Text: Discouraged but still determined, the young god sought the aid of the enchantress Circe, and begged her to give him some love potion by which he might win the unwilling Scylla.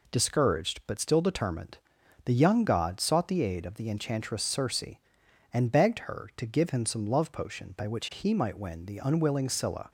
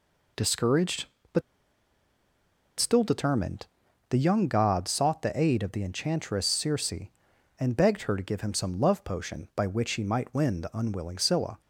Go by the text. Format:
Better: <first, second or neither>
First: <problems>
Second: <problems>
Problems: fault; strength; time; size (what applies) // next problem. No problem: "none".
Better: first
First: none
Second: pauses between "but" and "still"; strong; at 1.4 s; 1.3 s long